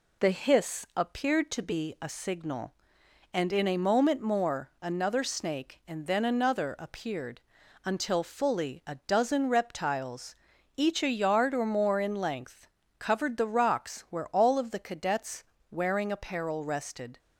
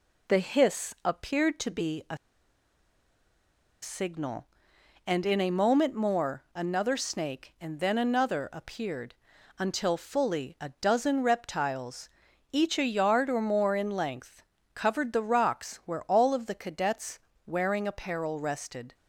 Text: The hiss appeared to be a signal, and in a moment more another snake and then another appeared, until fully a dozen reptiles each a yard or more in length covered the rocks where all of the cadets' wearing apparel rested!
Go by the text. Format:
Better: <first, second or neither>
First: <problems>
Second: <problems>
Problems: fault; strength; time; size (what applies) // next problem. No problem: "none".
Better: first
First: pauses between "reptiles" and "each"; at 10.3 s; 0.40 s long // pauses between "length" and "covered"; slight; at 12.6 s; 0.32 s long // pauses between "cadets" and "wearing"; slight; at 15.4 s; 0.26 s long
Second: pauses between "a" and "signal"; strong; at 2.1 s; 1.6 s long // pauses between "reptiles" and "each"; at 12.0 s; 0.42 s long // pauses between "length" and "covered"; slight; at 14.4 s; 0.32 s long // pauses between "cadets" and "wearing"; slight; at 17.1 s; 0.26 s long